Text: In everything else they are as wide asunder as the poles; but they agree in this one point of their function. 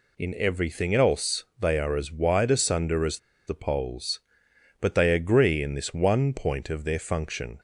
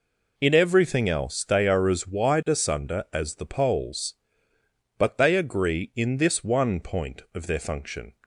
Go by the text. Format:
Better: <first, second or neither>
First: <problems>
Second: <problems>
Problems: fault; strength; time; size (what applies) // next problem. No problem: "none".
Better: second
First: pauses between "as" and "the"; slight; at 3.1 s; 0.28 s long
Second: none